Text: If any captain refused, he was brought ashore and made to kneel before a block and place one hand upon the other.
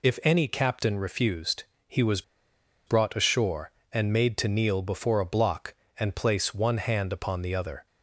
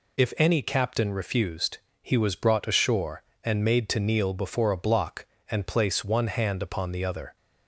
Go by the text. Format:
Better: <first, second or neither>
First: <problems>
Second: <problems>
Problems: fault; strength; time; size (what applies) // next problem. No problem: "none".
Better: second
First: pauses between "was" and "brought"; noticeable; at 2.2 s; 0.65 s long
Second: none